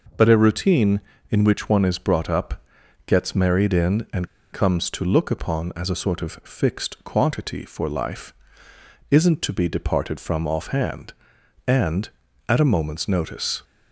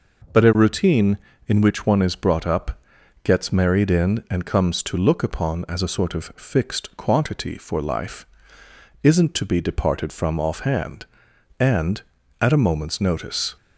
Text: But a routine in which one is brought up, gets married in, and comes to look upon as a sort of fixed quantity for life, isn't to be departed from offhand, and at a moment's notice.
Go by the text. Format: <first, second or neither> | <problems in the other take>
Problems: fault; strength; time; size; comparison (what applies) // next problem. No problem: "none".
second | pauses between "and" and "comes"; slight; at 4.2 s; 0.25 s long